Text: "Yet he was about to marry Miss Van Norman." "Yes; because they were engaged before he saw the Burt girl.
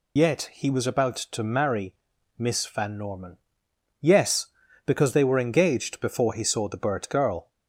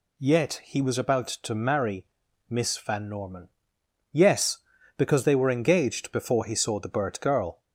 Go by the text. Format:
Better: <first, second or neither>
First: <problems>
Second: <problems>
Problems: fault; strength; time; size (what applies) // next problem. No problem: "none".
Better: second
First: loses the start of "Yet"; at 0.1 s; 80 ms // pauses between "marry" and "Miss"; at 1.9 s; 0.42 s long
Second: pauses between "marry" and "Miss"; at 2.0 s; 0.42 s long